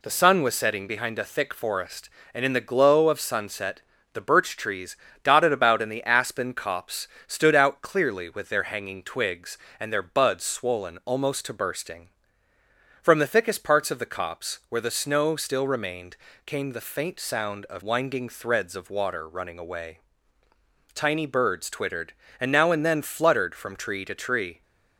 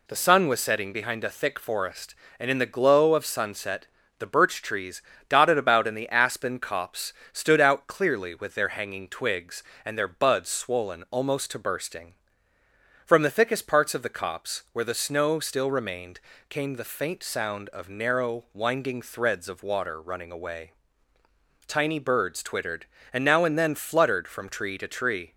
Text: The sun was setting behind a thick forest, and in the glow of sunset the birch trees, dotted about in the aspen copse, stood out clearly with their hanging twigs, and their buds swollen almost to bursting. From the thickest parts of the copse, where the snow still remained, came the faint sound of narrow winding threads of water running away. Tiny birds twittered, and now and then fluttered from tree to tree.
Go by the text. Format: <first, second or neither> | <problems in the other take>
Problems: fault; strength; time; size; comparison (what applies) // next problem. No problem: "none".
second | pauses between "sunset" and "the"; slight; at 3.8 s; 0.32 s long; slight in the second // skips "narrow"; at 17.8 s